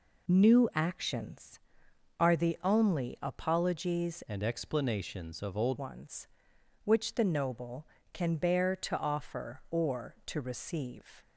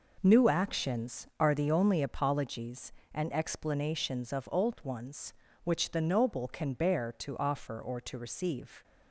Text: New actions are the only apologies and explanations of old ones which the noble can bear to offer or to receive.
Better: second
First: changes voice from "and" to "old"; from 4.2 to 5.7 s; 1.5 s long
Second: none

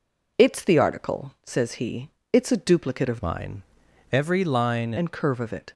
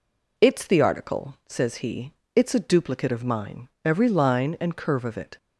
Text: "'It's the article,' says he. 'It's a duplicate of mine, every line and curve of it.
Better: second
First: changes voice from "mine" to "line"; from 3.2 to 4.9 s; 1.7 s long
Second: none

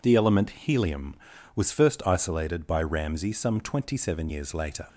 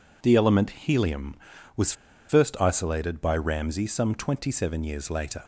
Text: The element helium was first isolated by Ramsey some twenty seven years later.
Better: first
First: none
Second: pauses between "was" and "first"; at 1.9 s; 0.36 s long

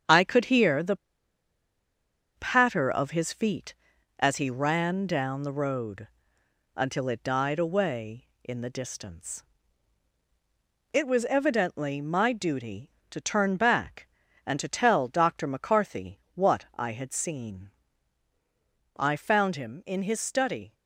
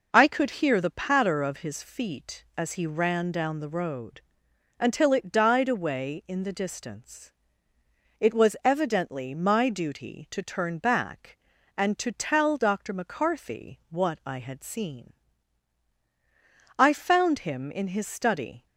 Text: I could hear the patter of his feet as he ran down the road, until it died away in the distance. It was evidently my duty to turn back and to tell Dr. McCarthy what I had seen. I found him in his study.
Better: second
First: starts louder than the rest; strong; until 2.4 s; 7.5 dB // pauses between "the" and "patter"; strong; at 0.9 s; 1.3 s long // pauses between "McCarthy" and "what"; slight; at 16.1 s; 0.16 s long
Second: none

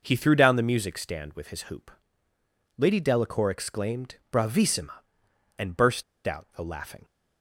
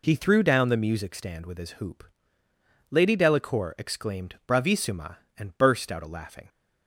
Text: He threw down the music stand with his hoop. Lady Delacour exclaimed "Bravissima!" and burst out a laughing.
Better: second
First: pauses between "exclaimed" and "Bravissima"; slight; at 4.1 s; 0.18 s long // pauses between "burst" and "out"; slight; at 6.0 s; 0.23 s long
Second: none

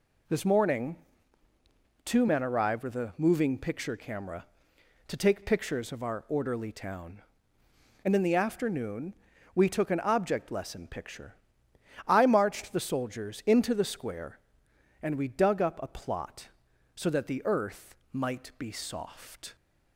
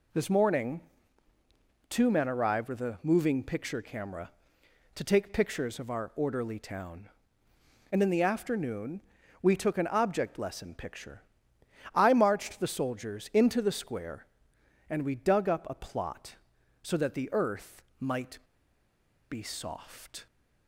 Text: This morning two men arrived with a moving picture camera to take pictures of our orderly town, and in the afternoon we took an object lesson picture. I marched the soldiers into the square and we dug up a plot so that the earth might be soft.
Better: first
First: pauses between "morning" and "two"; at 0.9 s; 1.0 s long // pauses between "afternoon" and "we"; at 9.1 s; 0.40 s long // pauses between "earth" and "might"; slight; at 17.9 s; 0.16 s long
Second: pauses between "morning" and "two"; at 0.8 s; 1.0 s long // pauses between "afternoon" and "we"; at 9.0 s; 0.40 s long // pauses between "earth" and "might"; slight; at 17.8 s; 0.16 s long // pauses between "might" and "be"; noticeable; at 18.3 s; 0.91 s long

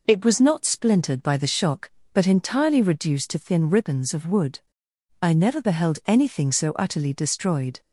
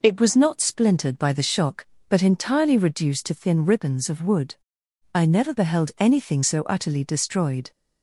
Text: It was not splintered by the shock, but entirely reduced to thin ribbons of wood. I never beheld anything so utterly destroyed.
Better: neither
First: none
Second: none

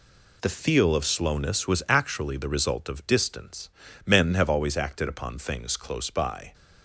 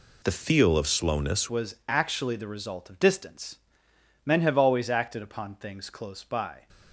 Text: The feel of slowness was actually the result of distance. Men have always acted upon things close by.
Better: first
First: none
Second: changes voice at "was"; from 1.5 s on; 5.1 s long

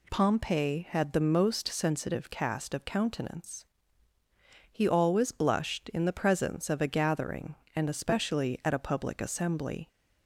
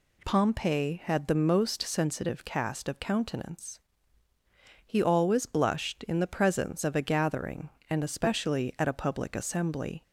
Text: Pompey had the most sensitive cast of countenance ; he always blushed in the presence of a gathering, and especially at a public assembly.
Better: neither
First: none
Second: none

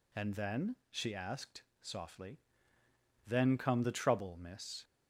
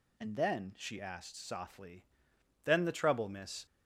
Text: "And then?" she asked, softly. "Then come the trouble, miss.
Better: first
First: none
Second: skips "come"; at 2.8 s

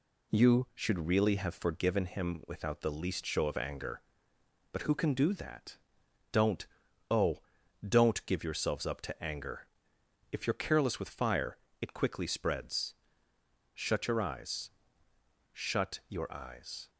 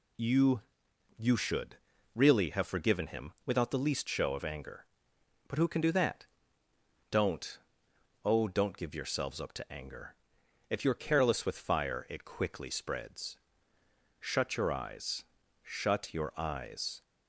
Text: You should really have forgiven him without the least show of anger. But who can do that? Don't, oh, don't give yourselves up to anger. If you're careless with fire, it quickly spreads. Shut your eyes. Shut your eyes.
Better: first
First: none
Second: says "You" twice; at 1.1 s // pauses between "should" and "really"; at 1.7 s; 0.38 s long

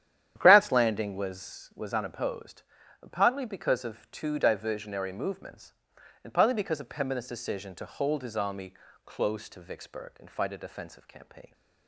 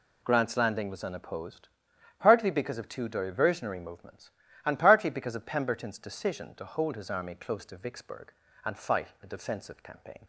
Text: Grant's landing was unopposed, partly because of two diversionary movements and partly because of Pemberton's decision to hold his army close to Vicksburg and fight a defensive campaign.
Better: second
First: starts louder than the rest; strong; until 1.3 s; 10.5 dB // says "was" twice; at 1.7 s // pauses between "army" and "close"; slight; at 8.7 s; 0.32 s long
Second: none

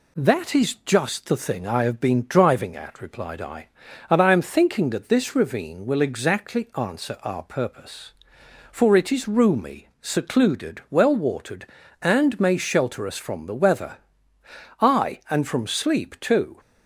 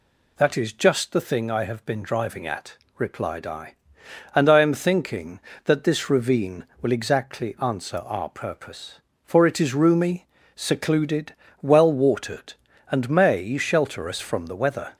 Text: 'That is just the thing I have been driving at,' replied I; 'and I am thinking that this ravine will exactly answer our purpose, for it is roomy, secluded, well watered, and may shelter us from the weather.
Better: second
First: goes on to say "Aye and from sleep too"; strong; from 14.7 s on; 1.8 s long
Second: none

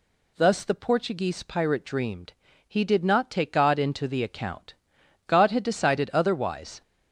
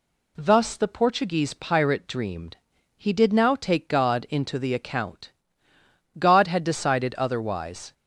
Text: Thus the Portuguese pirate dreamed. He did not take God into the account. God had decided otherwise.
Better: first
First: none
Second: says "now" for "not"; at 3.3 s

